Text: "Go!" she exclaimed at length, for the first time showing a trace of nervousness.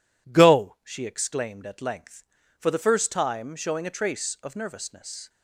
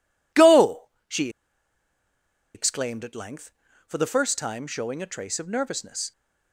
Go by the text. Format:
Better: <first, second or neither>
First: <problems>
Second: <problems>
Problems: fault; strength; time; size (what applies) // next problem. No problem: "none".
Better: first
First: none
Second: pauses between "she" and "exclaimed"; strong; at 1.2 s; 1.2 s long